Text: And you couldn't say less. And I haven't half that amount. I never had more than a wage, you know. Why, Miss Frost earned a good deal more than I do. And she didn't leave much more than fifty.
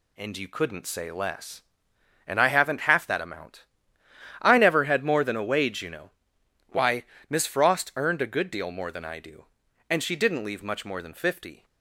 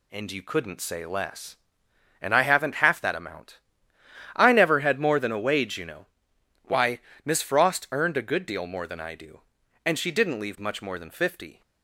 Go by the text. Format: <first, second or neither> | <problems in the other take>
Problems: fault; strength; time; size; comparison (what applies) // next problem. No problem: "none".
neither | none